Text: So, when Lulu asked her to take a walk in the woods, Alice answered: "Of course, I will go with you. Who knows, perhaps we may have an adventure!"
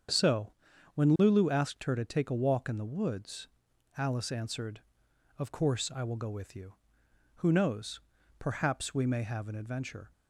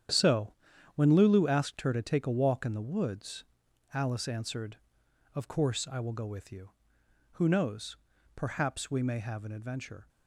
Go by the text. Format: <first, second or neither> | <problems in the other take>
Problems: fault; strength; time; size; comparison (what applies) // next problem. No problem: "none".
first | gets quieter; strong; throughout; 10 dB // starts louder than the rest; strong; until 1.5 s; 9.5 dB; strong in the first